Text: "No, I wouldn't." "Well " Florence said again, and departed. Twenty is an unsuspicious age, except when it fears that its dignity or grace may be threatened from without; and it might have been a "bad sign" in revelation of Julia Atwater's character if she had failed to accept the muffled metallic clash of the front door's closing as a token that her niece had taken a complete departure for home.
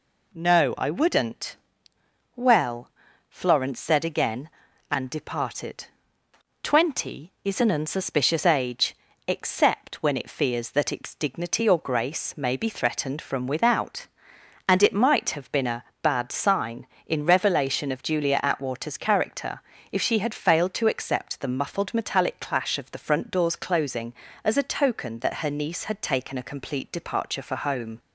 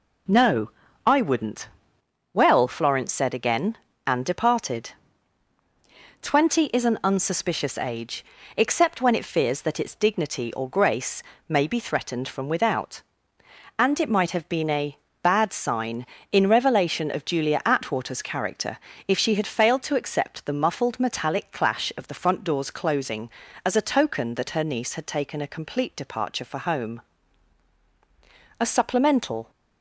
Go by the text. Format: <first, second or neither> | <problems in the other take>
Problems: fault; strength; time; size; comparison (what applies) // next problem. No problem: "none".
first | pauses between "grace" and "may"; slight; at 11.2 s; 0.24 s long // pauses between "a" and "bad"; slight; at 14.9 s; 0.26 s long; slight in the first // pauses between "character" and "if"; slight; at 18.7 s; 0.28 s long; slight in the first // goes on to say "A supplemental"; noticeable; from 28.5 s on; 0.92 s long